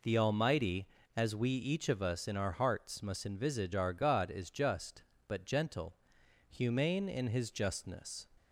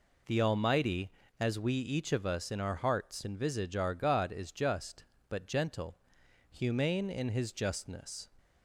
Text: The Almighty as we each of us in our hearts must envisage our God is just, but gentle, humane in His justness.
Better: first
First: none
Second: skips "must"; at 3.2 s

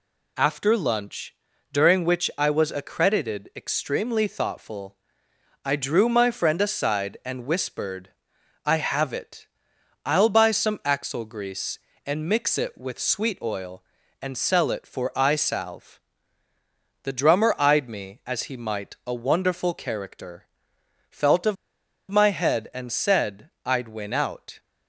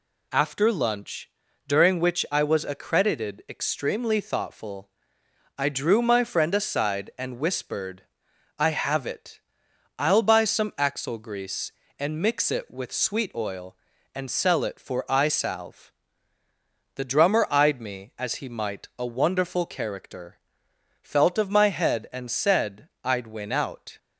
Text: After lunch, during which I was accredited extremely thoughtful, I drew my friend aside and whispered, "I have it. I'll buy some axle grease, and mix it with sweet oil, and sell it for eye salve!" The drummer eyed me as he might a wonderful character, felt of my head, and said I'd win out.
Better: second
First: pauses between "of" and "my"; noticeable; at 21.5 s; 0.55 s long // pauses between "said" and "I'd"; slight; at 23.4 s; 0.16 s long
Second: pauses between "said" and "I'd"; slight; at 22.8 s; 0.16 s long

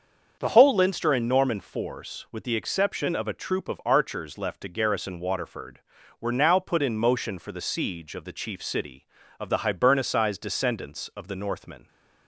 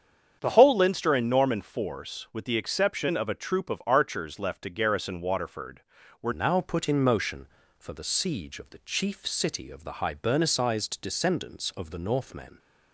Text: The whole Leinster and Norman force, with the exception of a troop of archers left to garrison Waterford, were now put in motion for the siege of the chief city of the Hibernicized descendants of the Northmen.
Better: first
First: starts louder than the rest; until 1.4 s; 6.5 dB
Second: starts louder than the rest; strong; until 1.4 s; 8 dB // changes voice at "now"; from 6.3 s on; 6.2 s long

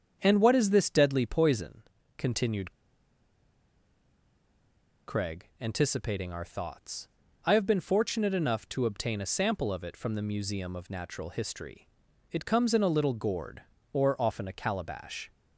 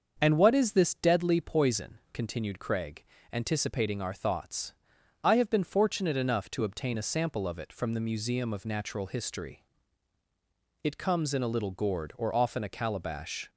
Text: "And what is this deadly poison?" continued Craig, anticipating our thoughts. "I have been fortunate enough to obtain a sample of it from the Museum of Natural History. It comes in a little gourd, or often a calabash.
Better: second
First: starts louder than the rest; strong; until 1.2 s; 7.5 dB // pauses between "continued" and "Craig"; strong; at 2.7 s; 2.3 s long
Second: starts louder than the rest; until 1.2 s; 6.5 dB

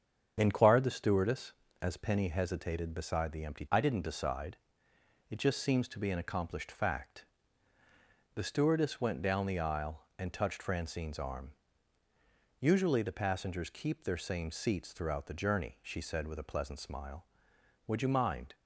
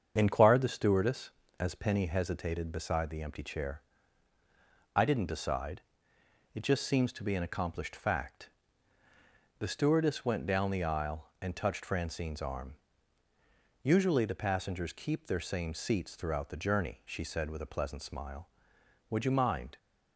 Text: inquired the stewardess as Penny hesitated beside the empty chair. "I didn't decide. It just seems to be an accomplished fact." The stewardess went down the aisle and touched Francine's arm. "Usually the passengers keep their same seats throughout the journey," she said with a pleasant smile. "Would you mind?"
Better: second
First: starts louder than the rest; strong; until 1.3 s; 7.5 dB // skips "chair"; at 3.6 s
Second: starts louder than the rest; strong; until 1.1 s; 7 dB

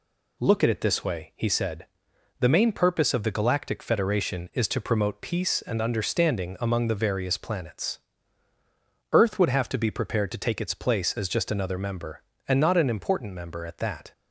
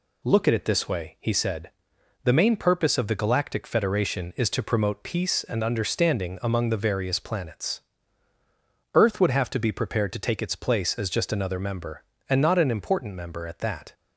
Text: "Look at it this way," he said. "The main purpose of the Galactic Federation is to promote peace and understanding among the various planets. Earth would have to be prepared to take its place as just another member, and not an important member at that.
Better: neither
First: none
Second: none

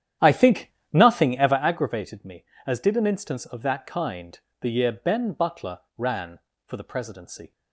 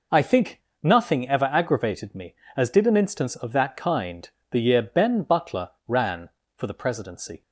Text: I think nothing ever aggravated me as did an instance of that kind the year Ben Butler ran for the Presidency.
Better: second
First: starts louder than the rest; strong; until 1.8 s; 10 dB // pauses between "think" and "nothing"; slight; at 0.7 s; 0.22 s long // pauses between "kind" and "the"; slight; at 4.3 s; 0.22 s long // pauses between "Butler" and "ran"; slight; at 5.7 s; 0.18 s long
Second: pauses between "think" and "nothing"; slight; at 0.6 s; 0.22 s long // pauses between "kind" and "the"; slight; at 4.2 s; 0.22 s long // pauses between "Butler" and "ran"; slight; at 5.6 s; 0.18 s long

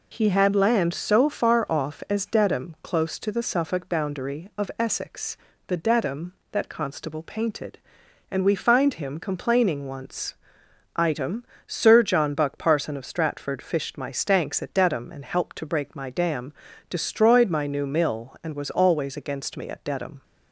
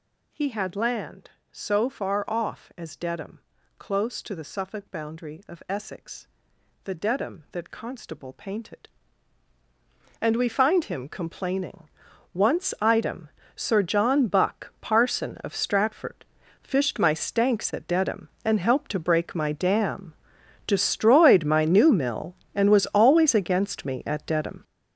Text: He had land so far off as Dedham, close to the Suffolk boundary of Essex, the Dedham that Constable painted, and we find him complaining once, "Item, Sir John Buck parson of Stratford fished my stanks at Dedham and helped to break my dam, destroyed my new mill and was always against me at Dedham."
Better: first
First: none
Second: gets louder; strong; throughout; 10 dB // pauses between "complaining" and "once"; at 11.8 s; 0.42 s long // pauses between "Stratford" and "fished"; at 16.2 s; 0.38 s long

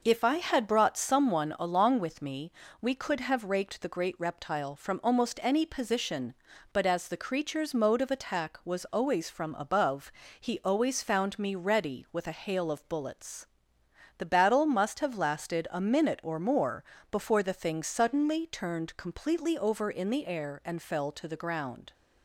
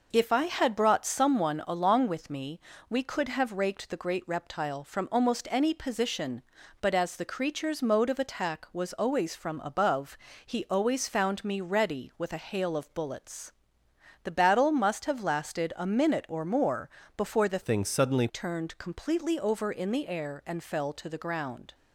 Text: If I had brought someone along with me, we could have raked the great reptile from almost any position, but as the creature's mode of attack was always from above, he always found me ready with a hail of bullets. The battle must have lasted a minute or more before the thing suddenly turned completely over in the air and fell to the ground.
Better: first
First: pauses between "more" and "before"; slight; at 16.8 s; 0.28 s long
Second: pauses between "more" and "before"; slight; at 16.8 s; 0.28 s long // changes voice from "thing" to "suddenly"; from 17.6 to 18.2 s; 0.6 s long

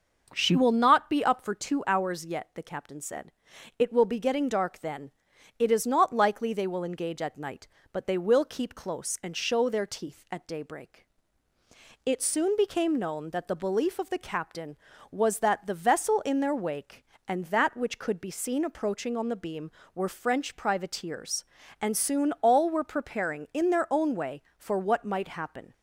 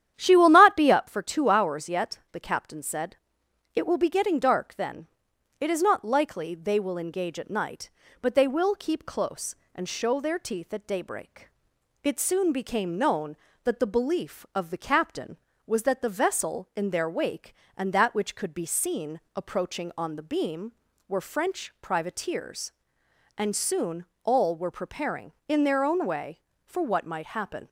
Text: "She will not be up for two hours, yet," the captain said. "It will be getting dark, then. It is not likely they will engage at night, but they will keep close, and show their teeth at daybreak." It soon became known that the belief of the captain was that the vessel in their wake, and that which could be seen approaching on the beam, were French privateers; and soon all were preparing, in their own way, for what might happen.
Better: first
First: none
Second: starts louder than the rest; strong; until 1.1 s; 10.5 dB // pauses between "soon" and "all"; slight; at 24.0 s; 0.16 s long

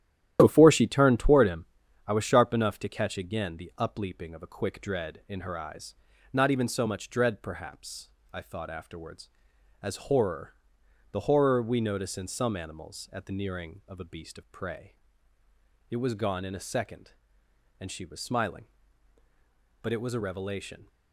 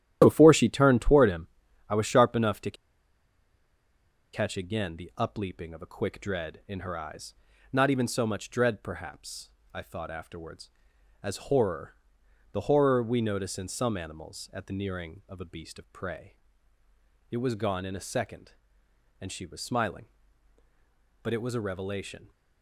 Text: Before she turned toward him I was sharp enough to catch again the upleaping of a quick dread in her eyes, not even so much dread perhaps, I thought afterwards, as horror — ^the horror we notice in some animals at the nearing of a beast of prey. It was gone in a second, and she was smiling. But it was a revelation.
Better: first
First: starts louder than the rest; strong; until 1.4 s; 12 dB // pauses between "him" and "I"; at 1.6 s; 0.40 s long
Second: starts louder than the rest; strong; until 1.2 s; 12 dB // pauses between "him" and "I"; at 1.4 s; 0.40 s long // pauses between "to" and "catch"; strong; at 2.7 s; 1.6 s long

